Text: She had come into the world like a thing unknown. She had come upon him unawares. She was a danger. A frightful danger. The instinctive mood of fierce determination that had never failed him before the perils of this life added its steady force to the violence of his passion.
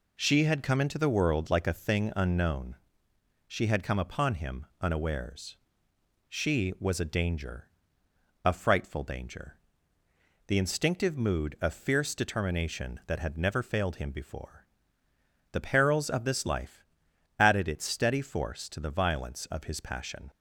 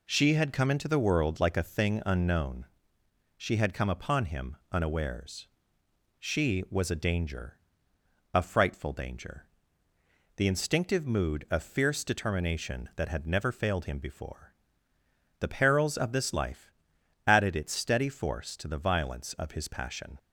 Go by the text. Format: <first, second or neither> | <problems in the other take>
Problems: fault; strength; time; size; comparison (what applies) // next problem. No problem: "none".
neither | pauses between "him" and "unawares"; slight; the same in both // pauses between "before" and "the"; noticeable; the same in both // pauses between "life" and "added"; noticeable; the same in both